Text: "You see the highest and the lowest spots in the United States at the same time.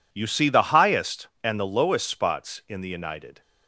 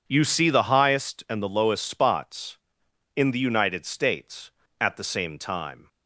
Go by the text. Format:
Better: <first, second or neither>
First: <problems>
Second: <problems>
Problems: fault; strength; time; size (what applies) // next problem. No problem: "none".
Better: second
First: stops before "States at the same time"; at 3.4 s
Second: none